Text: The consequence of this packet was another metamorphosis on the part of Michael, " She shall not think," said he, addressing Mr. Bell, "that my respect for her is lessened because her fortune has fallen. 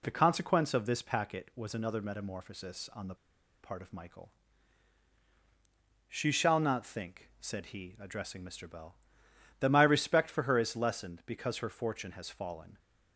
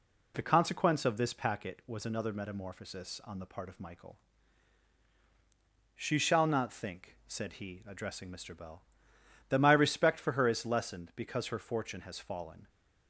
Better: second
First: pauses between "the" and "part"; noticeable; at 3.1 s; 0.47 s long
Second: none

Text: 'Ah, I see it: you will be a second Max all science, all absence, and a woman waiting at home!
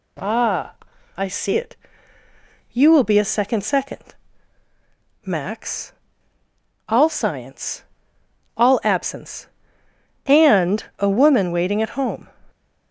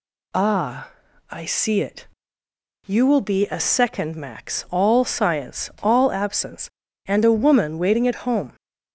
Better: second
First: says "second" twice; at 3.6 s // pauses between "Max" and "all"; noticeable; at 5.9 s; 0.96 s long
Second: none

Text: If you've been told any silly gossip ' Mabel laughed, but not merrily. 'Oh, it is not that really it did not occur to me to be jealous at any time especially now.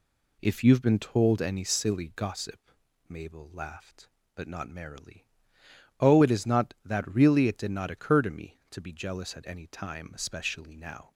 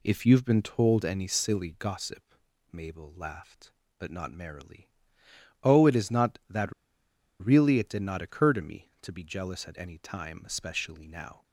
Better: first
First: none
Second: pauses between "that" and "really"; noticeable; at 6.7 s; 0.68 s long

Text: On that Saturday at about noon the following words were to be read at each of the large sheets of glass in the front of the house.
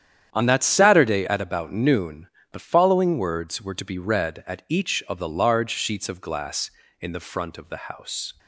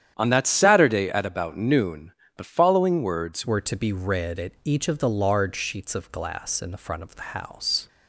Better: first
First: starts louder than the rest; strong; until 1.3 s; 9.5 dB // pauses between "noon" and "the"; slight; at 2.2 s; 0.24 s long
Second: starts louder than the rest; strong; until 1.1 s; 9.5 dB // pauses between "noon" and "the"; slight; at 2.1 s; 0.24 s long // changes voice at "were"; from 3.4 s on; 4.4 s long

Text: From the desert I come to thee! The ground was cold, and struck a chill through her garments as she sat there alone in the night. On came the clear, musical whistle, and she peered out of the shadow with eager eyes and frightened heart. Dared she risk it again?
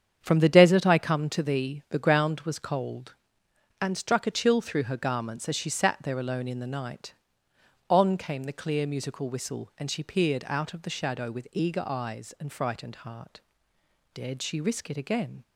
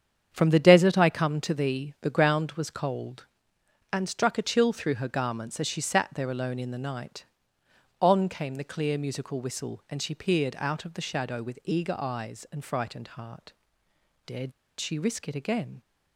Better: first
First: starts louder than the rest; strong; until 1.2 s; 8 dB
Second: starts louder than the rest; strong; until 1.3 s; 8 dB // pauses between "Dared" and "she"; slight; at 14.5 s; 0.28 s long

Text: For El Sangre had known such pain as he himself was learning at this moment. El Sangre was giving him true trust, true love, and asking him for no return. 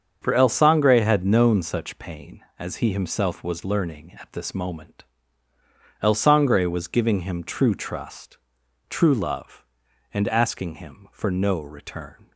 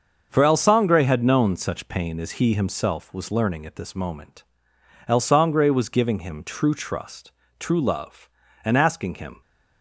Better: first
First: starts louder than the rest; until 1.2 s; 7 dB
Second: starts louder than the rest; until 1.3 s; 6.5 dB // stops before "for no return"; at 9.4 s

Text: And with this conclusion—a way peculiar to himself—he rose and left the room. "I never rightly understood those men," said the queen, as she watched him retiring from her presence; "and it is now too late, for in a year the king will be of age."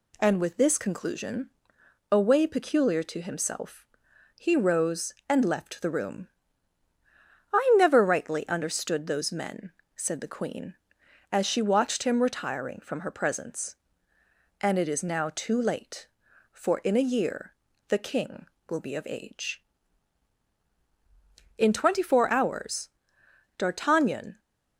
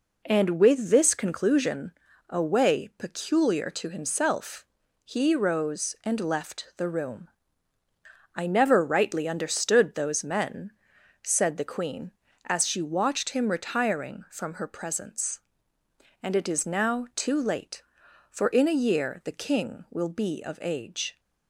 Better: second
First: pauses between "year" and "the"; slight; at 17.5 s; 0.34 s long // goes on to say "In twenty four hours D'Artagnan"; strong; from 21.5 s on; 2.8 s long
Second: none

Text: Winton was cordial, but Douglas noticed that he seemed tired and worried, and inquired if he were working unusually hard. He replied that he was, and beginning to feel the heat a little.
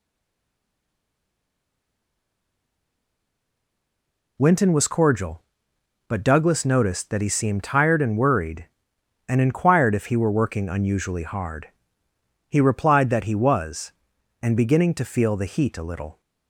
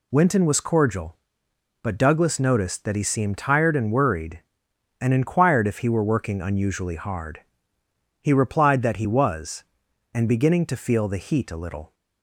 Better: second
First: stays silent before the first word; strong; until 4.3 s; 4.3 s long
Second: none

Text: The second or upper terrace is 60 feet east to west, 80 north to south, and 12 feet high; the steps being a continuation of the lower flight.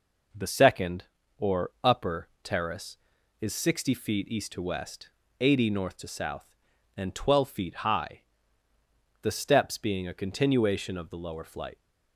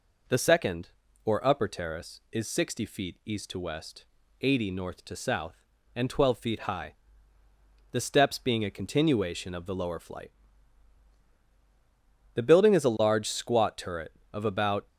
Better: first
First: none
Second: goes on to say "The building is a large squat turret of about"; strong; from 12.3 s on; 2.5 s long

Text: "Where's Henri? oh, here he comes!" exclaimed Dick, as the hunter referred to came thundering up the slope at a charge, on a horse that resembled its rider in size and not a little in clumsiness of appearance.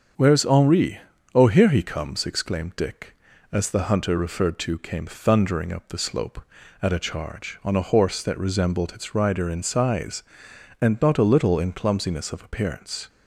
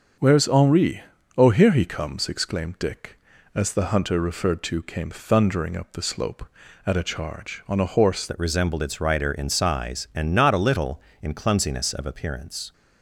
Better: first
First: starts louder than the rest; until 1.5 s; 7 dB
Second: starts louder than the rest; until 1.5 s; 6.5 dB // changes voice at "that"; from 8.2 s on; 4.5 s long

